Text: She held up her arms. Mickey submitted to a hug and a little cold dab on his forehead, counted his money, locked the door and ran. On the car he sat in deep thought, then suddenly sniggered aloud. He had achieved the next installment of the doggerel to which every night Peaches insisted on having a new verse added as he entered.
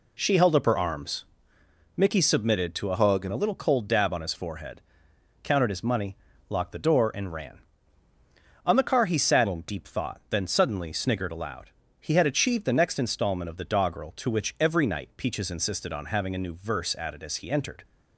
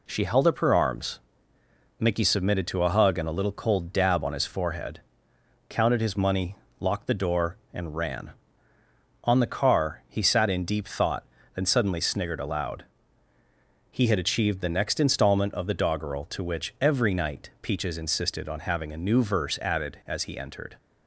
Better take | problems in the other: second | changes voice from "hug" to "and"; from 2.9 to 3.3 s; 0.4 s long

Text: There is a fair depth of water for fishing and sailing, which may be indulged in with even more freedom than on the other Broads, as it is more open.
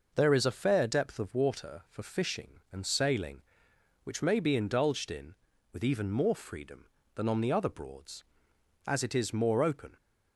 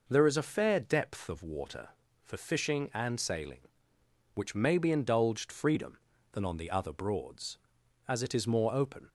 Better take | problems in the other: first | skips "in with even more"; at 5.5 s

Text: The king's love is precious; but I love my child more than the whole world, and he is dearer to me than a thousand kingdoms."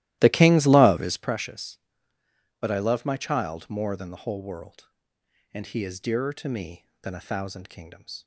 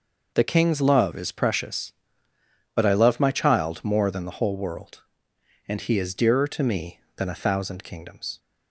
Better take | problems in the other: second | starts louder than the rest; strong; until 1.4 s; 15.5 dB

